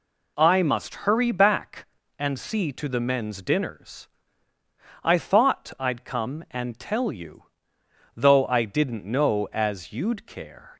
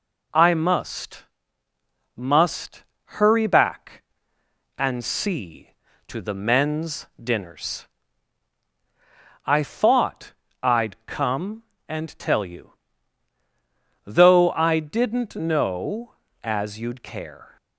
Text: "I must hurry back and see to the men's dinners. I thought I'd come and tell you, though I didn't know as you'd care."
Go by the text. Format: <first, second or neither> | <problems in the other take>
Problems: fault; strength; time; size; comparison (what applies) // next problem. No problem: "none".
first | says "must" twice; at 2.1 s // pauses between "thought" and "I'd"; slight; at 10.3 s; 0.30 s long